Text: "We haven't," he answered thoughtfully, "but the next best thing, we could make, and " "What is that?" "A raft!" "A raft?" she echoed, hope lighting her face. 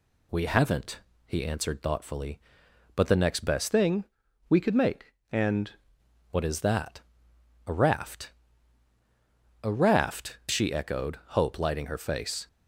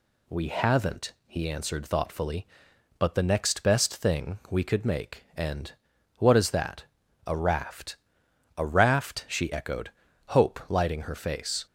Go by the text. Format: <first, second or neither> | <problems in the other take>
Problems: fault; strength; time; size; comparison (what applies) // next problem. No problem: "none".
second | changes voice from "thing" to "and"; from 3.7 to 5.7 s; 2.0 s long